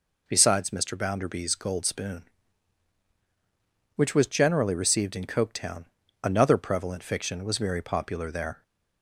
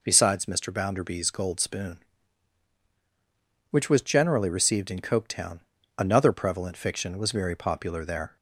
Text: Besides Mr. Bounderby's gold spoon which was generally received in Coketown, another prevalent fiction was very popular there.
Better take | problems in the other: neither | none

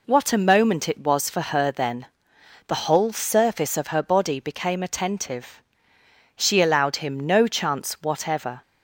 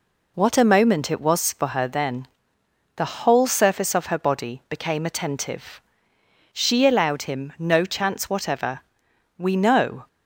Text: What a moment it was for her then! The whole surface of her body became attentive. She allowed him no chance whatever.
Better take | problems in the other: first | goes on to say "We know"; noticeable; from 9.3 s on; 0.70 s long

